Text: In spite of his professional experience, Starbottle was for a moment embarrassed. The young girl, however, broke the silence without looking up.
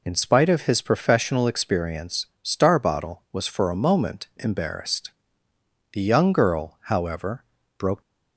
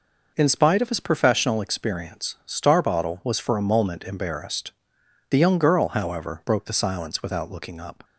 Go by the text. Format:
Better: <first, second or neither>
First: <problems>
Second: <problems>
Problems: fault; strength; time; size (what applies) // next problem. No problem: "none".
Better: second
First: stops before "the silence without looking up"; at 8.0 s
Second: none